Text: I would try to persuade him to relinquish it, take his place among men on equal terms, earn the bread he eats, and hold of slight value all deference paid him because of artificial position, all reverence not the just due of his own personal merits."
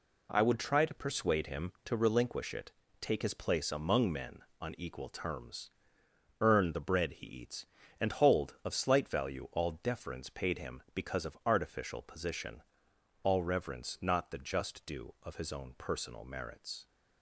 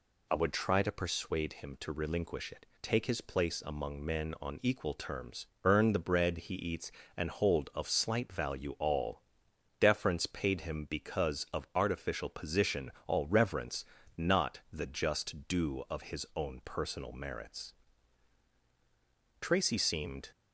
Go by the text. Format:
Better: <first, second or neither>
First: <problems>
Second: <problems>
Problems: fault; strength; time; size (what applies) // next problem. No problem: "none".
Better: first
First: none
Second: pauses between "all" and "deference"; noticeable; at 9.2 s; 0.56 s long // pauses between "reverence" and "not"; slight; at 13.8 s; 0.34 s long // goes on to say "Tracy seemed"; noticeable; from 19.4 s on; 0.88 s long